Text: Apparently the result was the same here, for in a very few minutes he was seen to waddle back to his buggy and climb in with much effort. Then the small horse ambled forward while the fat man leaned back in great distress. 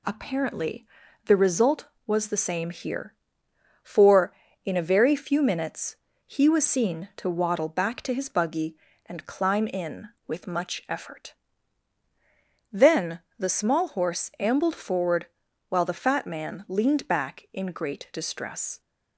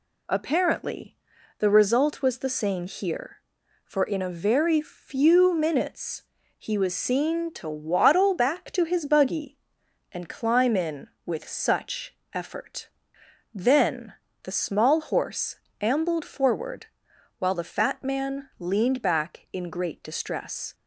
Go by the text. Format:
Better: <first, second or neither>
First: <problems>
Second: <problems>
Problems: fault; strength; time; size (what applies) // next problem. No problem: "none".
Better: first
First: pauses between "Apparently" and "the"; at 0.8 s; 0.40 s long // pauses between "minutes" and "he"; slight; at 5.9 s; 0.30 s long // pauses between "Then" and "the"; slight; at 13.2 s; 0.18 s long // pauses between "forward" and "while"; at 15.2 s; 0.42 s long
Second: pauses between "Apparently" and "the"; at 1.1 s; 0.42 s long // pauses between "minutes" and "he"; slight; at 6.2 s; 0.36 s long // says "such" for "much"; at 11.4 s // pauses between "Then" and "the"; slight; at 14.1 s; 0.28 s long // pauses between "horse" and "ambled"; slight; at 15.5 s; 0.24 s long // pauses between "forward" and "while"; noticeable; at 16.8 s; 0.52 s long